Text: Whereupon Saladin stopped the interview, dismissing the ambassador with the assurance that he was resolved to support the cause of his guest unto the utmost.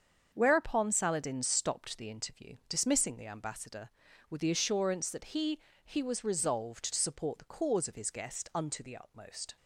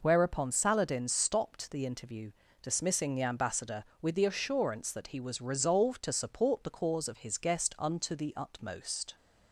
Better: second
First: starts louder than the rest; until 1.3 s; 7 dB // says "he" twice; at 5.8 s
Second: none

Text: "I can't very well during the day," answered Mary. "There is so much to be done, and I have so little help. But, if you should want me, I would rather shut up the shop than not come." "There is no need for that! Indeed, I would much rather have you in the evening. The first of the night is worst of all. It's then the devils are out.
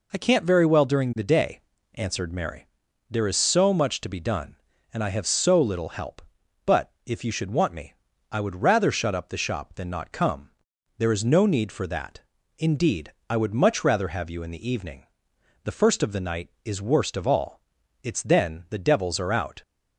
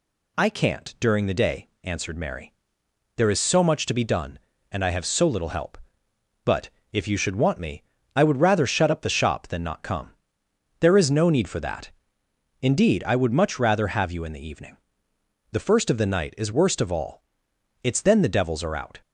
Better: first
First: none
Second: skips "very well"; at 0.9 s

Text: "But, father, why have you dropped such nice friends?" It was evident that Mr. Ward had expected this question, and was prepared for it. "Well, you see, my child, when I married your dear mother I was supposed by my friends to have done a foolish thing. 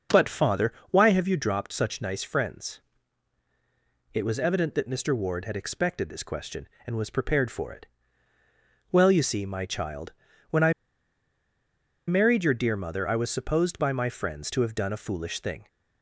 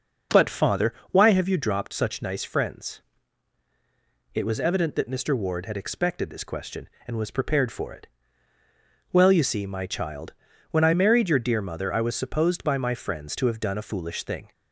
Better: second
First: starts louder than the rest; noticeable; until 1.2 s; 6 dB // pauses between "I" and "married"; strong; at 10.7 s; 1.3 s long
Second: starts louder than the rest; noticeable; until 1.4 s; 6 dB

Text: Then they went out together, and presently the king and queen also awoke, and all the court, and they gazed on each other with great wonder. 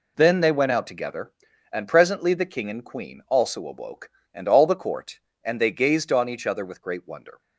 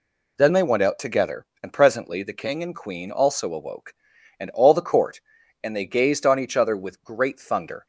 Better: first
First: none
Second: says "thunder" for "wonder"; at 7.3 s

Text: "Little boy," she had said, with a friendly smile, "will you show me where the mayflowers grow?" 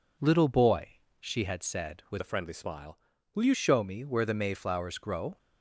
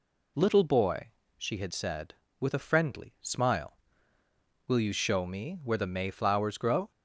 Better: second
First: changes voice from "a" to "you"; from 2.1 to 3.5 s; 1.4 s long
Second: none

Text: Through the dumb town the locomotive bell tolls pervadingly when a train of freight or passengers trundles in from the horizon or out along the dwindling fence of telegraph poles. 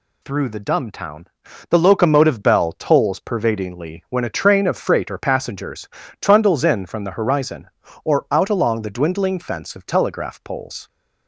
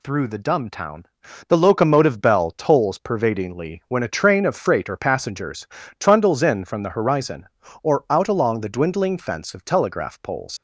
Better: first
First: pauses between "town" and "the"; at 1.2 s; 0.44 s long // pauses between "passengers" and "trundles"; slight; at 5.8 s; 0.32 s long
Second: pauses between "town" and "the"; at 1.0 s; 0.44 s long // pauses between "passengers" and "trundles"; slight; at 5.6 s; 0.32 s long // leaves "poles" unfinished; at 10.5 s; 95 ms

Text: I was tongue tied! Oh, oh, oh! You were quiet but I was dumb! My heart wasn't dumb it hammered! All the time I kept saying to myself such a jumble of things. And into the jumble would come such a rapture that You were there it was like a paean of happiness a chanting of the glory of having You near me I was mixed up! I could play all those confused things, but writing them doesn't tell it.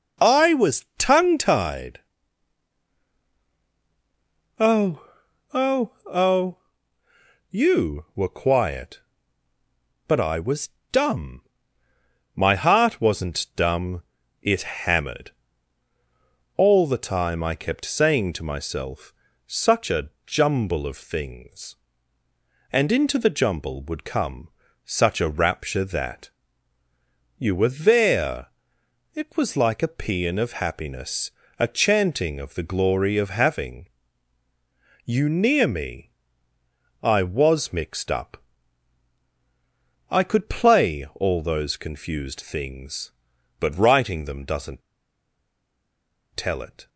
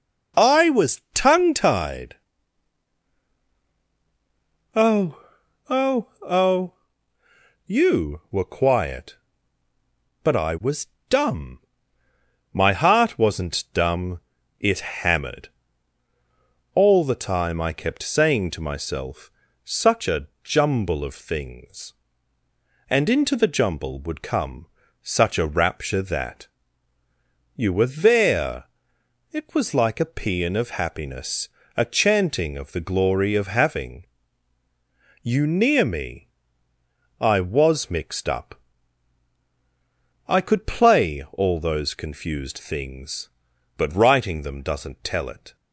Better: second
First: pauses between "was" and "dumb"; slight; at 10.6 s; 0.20 s long // pauses between "dumb" and "it"; at 14.0 s; 0.40 s long // pauses between "myself" and "such"; slight; at 19.1 s; 0.34 s long // pauses between "a" and "jumble"; slight; at 20.0 s; 0.18 s long // pauses between "come" and "such"; slight; at 24.4 s; 0.36 s long // pauses between "that" and "You"; at 26.2 s; 1.0 s long // pauses between "there" and "it"; noticeable; at 28.4 s; 0.66 s long // pauses between "happiness" and "a"; slight; at 31.3 s; 0.26 s long // pauses between "having" and "You"; at 33.8 s; 1.1 s long // pauses between "me" and "I"; noticeable; at 36.1 s; 0.90 s long // pauses between "doesn't" and "tell"; strong; at 44.8 s; 1.5 s long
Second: pauses between "was" and "dumb"; slight; at 10.8 s; 0.20 s long // pauses between "dumb" and "it"; at 14.1 s; 0.40 s long // pauses between "myself" and "such"; slight; at 19.2 s; 0.34 s long // pauses between "a" and "jumble"; slight; at 20.2 s; 0.18 s long // pauses between "come" and "such"; slight; at 24.6 s; 0.36 s long // pauses between "that" and "You"; at 26.4 s; 1.0 s long // pauses between "there" and "it"; noticeable; at 28.6 s; 0.66 s long // pauses between "happiness" and "a"; slight; at 31.4 s; 0.26 s long // pauses between "having" and "You"; at 34.0 s; 1.1 s long // pauses between "me" and "I"; noticeable; at 36.2 s; 0.90 s long

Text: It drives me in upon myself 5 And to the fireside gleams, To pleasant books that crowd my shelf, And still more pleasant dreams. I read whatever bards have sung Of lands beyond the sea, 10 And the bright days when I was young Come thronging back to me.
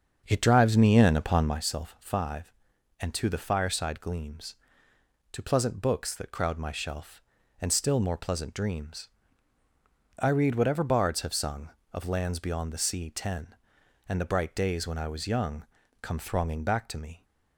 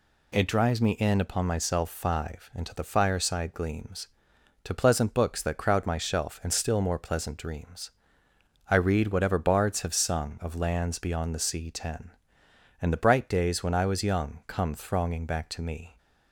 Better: second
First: starts louder than the rest; until 1.6 s; 6.5 dB // pauses between "young" and "Come"; slight; at 15.6 s; 0.36 s long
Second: none

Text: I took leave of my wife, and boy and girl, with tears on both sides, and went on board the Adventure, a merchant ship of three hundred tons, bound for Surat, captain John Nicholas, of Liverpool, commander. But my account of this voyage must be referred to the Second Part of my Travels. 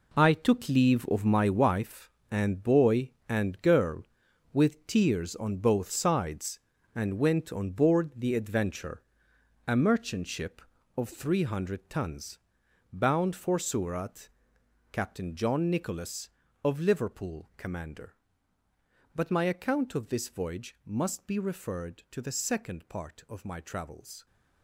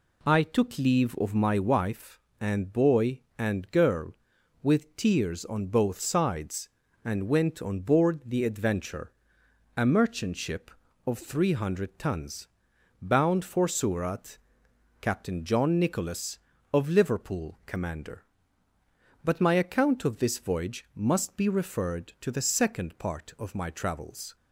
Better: second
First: gets quieter; strong; throughout; 10.5 dB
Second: none

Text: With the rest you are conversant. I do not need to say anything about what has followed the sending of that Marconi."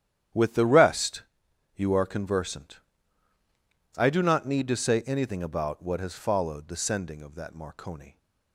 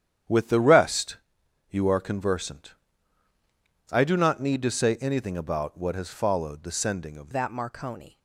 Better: first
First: starts louder than the rest; strong; until 1.8 s; 10.5 dB // pauses between "rest" and "you"; noticeable; at 1.2 s; 0.52 s long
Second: starts louder than the rest; strong; until 1.8 s; 9.5 dB // pauses between "rest" and "you"; noticeable; at 1.1 s; 0.52 s long // changes voice at "that"; from 7.3 s on; 0.8 s long

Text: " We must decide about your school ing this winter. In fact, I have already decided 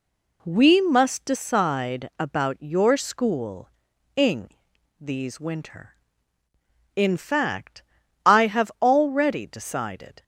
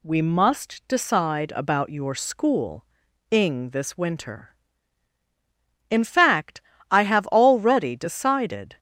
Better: second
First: pauses between "school" and "ing"; noticeable; at 3.6 s; 0.46 s long // says "these" for "this"; at 4.9 s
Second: pauses between "school" and "ing"; noticeable; at 2.8 s; 0.46 s long

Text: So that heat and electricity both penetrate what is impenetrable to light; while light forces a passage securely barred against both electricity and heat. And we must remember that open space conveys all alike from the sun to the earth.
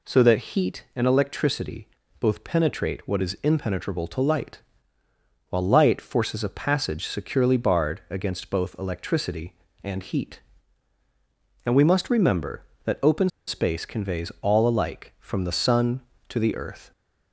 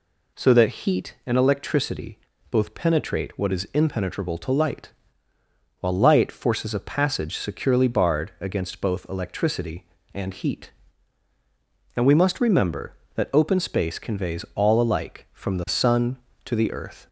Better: second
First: pauses between "electricity" and "both"; slight; at 1.8 s; 0.32 s long // pauses between "open" and "space"; slight; at 13.2 s; 0.19 s long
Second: pauses between "electricity" and "both"; slight; at 2.1 s; 0.32 s long

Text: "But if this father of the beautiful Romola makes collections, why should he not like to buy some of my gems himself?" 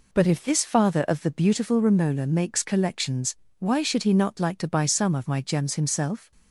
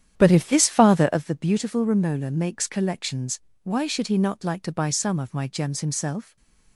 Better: first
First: none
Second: starts louder than the rest; strong; until 1.2 s; 10 dB

